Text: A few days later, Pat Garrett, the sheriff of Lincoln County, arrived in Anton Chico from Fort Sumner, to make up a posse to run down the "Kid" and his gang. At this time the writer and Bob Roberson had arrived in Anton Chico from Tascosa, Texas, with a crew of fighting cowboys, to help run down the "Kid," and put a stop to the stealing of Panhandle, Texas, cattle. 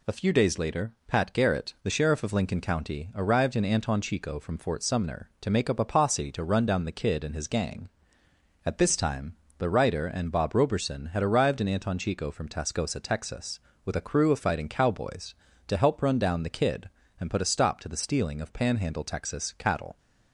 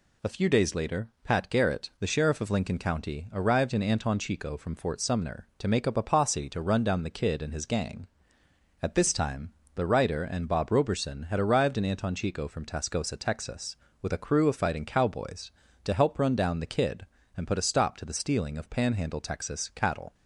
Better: neither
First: pauses between "time" and "the"; slight; at 9.3 s; 0.24 s long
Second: pauses between "time" and "the"; slight; at 9.5 s; 0.24 s long

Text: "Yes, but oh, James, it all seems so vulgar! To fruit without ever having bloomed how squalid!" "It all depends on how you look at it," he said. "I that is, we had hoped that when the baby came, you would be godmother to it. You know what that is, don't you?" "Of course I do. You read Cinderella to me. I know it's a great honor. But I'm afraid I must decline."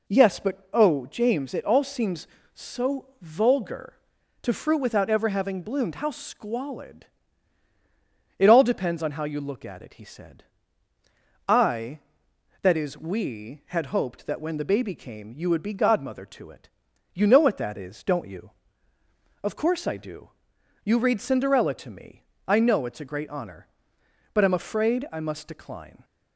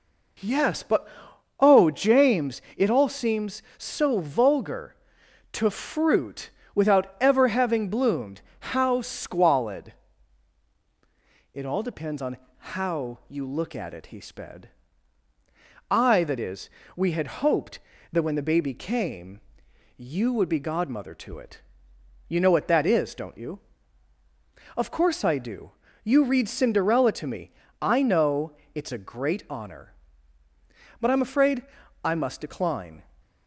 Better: first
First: none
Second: pauses between "but" and "oh"; noticeable; at 1.0 s; 0.54 s long // pauses between "fruit" and "without"; slight; at 6.4 s; 0.24 s long // pauses between "bloomed" and "how"; slight; at 8.4 s; 0.18 s long // pauses between "on" and "how"; slight; at 12.3 s; 0.22 s long // says "sped" for "said"; at 14.1 s // pauses between "know" and "it's"; slight; at 28.5 s; 0.22 s long // pauses between "afraid" and "I"; at 31.6 s; 0.40 s long

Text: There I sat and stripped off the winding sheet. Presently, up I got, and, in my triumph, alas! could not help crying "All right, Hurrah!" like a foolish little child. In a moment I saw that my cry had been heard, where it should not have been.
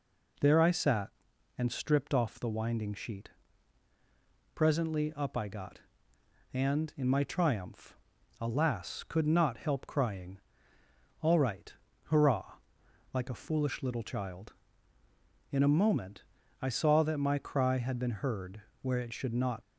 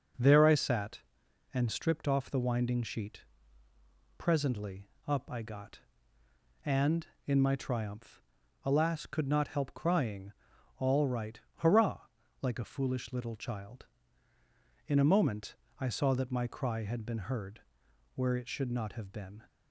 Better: second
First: pauses between "crying" and "All"; noticeable; at 10.3 s; 0.82 s long // pauses between "moment" and "I"; at 16.2 s; 0.38 s long // stops before "have been"; at 19.6 s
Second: pauses between "crying" and "All"; noticeable; at 10.3 s; 0.46 s long // pauses between "moment" and "I"; slight; at 15.5 s; 0.26 s long

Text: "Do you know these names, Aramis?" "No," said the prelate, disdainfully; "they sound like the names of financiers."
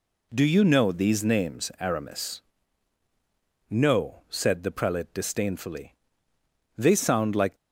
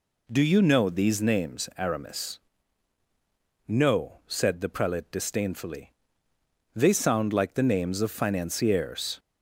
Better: second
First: stops before "the names of financiers"; at 7.5 s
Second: none

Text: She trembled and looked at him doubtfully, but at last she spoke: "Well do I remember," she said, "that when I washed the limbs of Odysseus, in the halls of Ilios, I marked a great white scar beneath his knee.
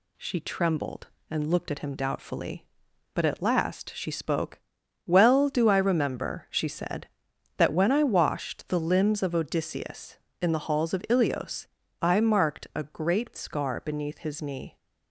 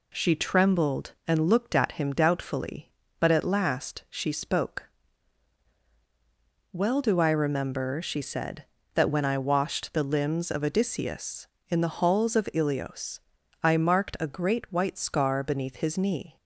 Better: second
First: skips "white"; at 13.3 s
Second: none

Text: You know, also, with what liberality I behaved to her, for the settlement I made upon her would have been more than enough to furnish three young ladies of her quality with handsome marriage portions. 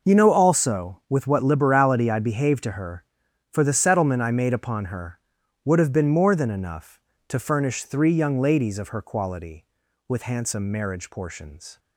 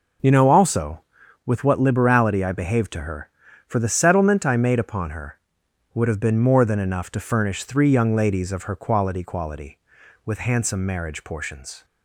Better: first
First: none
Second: says "quality" twice; at 9.2 s

